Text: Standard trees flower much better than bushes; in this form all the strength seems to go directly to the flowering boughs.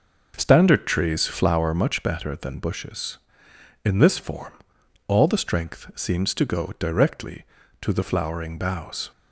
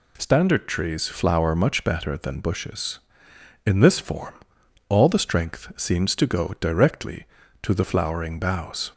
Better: second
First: starts louder than the rest; noticeable; until 1.6 s; 5.5 dB // pauses between "form" and "all"; noticeable; at 4.5 s; 0.56 s long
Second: pauses between "form" and "all"; noticeable; at 4.3 s; 0.56 s long

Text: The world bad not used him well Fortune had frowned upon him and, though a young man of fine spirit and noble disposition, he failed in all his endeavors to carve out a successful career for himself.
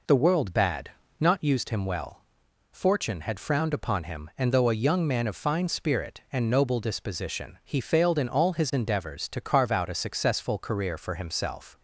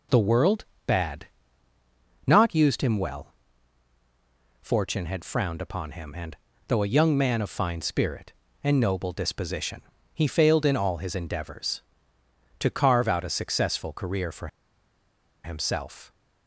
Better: first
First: pauses between "bad" and "not"; slight; at 0.9 s; 0.28 s long // pauses between "well" and "Fortune"; noticeable; at 2.2 s; 0.50 s long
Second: pauses between "world" and "bad"; slight; at 0.6 s; 0.24 s long // pauses between "bad" and "not"; at 1.2 s; 1.0 s long // pauses between "well" and "Fortune"; strong; at 3.3 s; 1.2 s long // pauses between "for" and "himself"; noticeable; at 14.4 s; 0.96 s long

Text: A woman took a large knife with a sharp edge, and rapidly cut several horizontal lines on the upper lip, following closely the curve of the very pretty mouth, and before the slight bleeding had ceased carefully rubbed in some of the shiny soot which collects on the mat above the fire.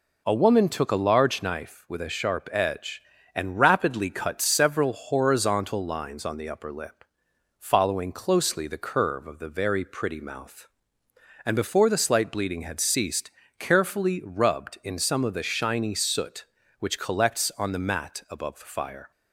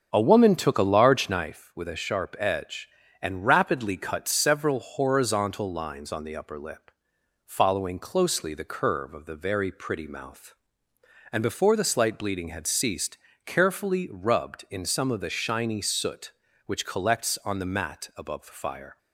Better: first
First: pauses between "ceased" and "carefully"; slight; at 13.3 s; 0.26 s long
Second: starts louder than the rest; strong; until 1.6 s; 8 dB // pauses between "ceased" and "carefully"; slight; at 13.1 s; 0.26 s long

